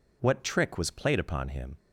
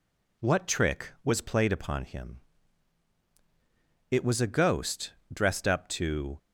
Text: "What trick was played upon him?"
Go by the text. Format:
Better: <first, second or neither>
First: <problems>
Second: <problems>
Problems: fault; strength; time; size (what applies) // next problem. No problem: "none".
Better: first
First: none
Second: goes on to say "It was a ghost dressed up to"; strong; from 4.1 s on; 2.2 s long